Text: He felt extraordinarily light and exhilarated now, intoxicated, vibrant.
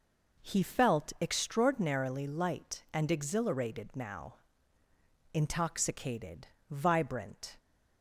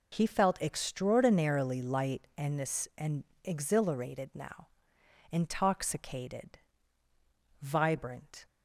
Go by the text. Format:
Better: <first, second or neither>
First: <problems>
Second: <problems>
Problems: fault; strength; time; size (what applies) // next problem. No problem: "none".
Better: first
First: none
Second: says "and" twice; at 2.9 s